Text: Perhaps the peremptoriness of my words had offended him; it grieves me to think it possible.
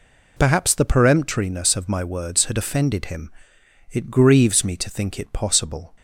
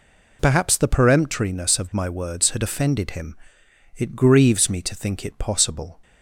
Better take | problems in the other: neither | none

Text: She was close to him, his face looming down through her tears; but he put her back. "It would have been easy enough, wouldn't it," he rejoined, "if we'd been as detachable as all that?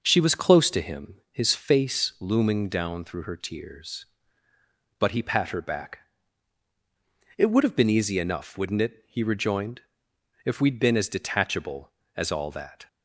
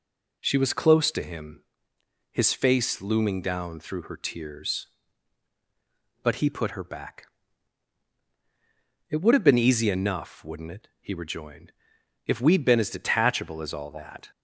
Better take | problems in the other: second | says "pat" for "put"; at 5.2 s

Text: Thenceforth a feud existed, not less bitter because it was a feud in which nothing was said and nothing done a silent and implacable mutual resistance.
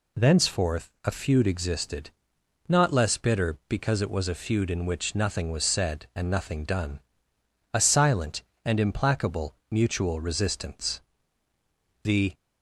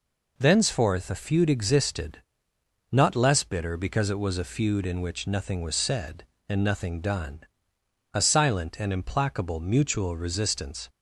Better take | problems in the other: second | pauses between "done" and "a"; noticeable; at 7.0 s; 0.74 s long; noticeable in the second // pauses between "implacable" and "mutual"; slight; at 9.5 s; 0.16 s long // goes on to say "The"; slight; from 12.0 s on; 0.30 s long

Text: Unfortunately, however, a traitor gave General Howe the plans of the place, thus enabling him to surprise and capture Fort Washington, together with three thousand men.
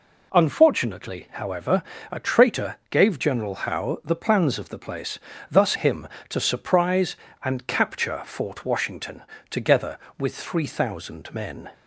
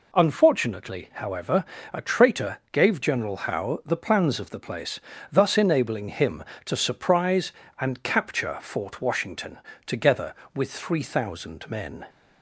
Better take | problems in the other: second | skips "enabling"; at 5.7 s

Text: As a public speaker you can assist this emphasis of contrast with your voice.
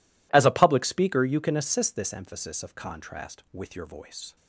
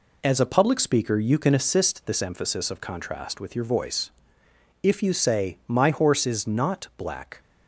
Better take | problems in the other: first | goes on to say "If you say My horse is not black"; strong; from 4.8 s on; 2.5 s long

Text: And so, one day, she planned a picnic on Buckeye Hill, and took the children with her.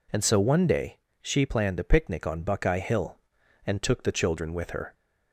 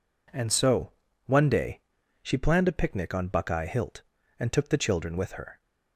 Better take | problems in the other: first | says "Hilt" for "Hill"; at 3.6 s

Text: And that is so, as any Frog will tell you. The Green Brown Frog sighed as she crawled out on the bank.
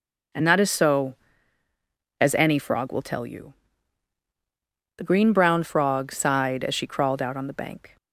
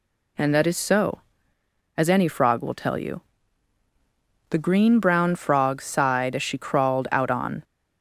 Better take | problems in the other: first | stops before "the bank"; at 7.6 s

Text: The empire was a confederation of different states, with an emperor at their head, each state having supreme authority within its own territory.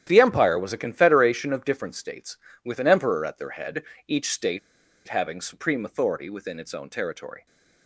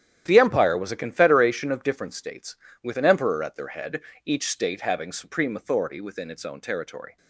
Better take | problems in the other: second | starts louder than the rest; strong; until 1.0 s; 10.5 dB; strong in the second // pauses between "state" and "having"; noticeable; at 4.5 s; 0.48 s long

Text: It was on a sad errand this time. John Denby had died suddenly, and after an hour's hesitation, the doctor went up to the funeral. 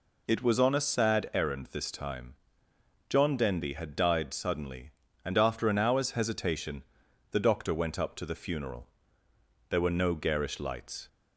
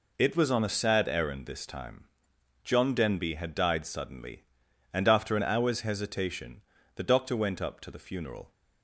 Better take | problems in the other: second | goes on to say "There were no garish lights"; from 9.6 s on; 1.3 s long

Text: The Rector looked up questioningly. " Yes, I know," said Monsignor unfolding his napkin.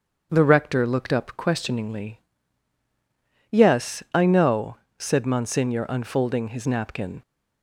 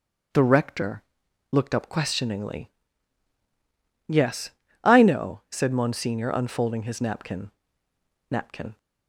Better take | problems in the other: first | pauses between "Rector" and "looked"; noticeable; at 1.0 s; 0.50 s long // says "napkin" twice; at 8.2 s

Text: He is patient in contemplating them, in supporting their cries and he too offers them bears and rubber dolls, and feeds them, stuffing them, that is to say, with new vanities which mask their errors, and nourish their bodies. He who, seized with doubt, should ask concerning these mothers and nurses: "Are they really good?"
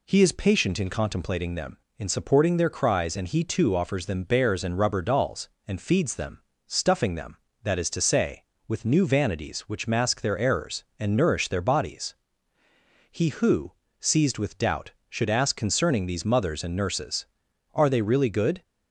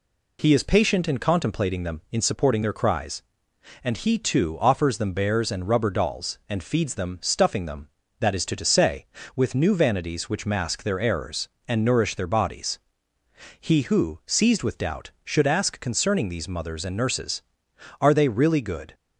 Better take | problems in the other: first | says "to" twice; at 8.5 s

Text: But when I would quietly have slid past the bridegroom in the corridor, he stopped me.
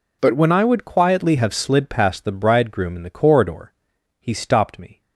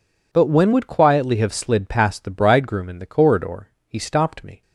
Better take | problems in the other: first | skips "I"; at 0.7 s

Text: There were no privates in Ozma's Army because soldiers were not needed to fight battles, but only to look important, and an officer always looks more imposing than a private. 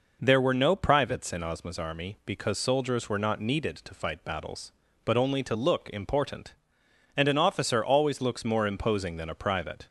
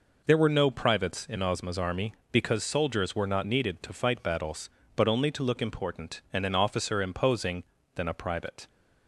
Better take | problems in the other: first | skips "always looks more"; at 7.0 s

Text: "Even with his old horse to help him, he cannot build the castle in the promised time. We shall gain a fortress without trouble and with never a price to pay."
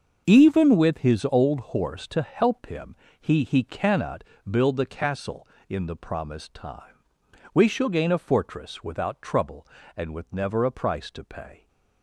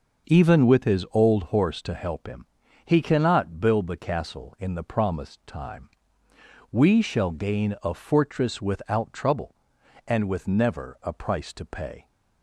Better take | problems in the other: second | starts louder than the rest; until 1.3 s; 6.5 dB // says "he" twice; at 3.4 s // pauses between "cannot" and "build"; slight; at 4.2 s; 0.26 s long

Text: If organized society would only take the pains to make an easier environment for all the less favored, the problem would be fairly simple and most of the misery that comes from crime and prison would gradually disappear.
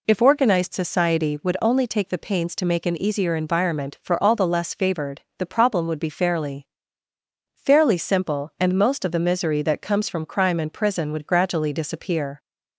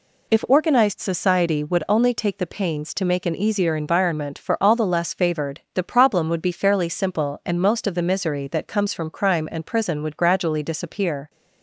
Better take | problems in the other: second | says "fairly" twice; at 7.5 s

